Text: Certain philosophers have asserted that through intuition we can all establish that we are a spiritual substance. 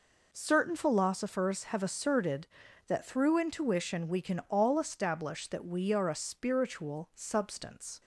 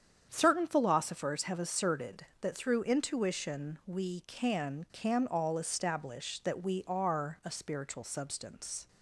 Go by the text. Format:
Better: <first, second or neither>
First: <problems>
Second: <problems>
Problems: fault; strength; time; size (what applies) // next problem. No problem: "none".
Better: first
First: none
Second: starts louder than the rest; strong; until 1.3 s; 8 dB // says "can" twice; at 4.9 s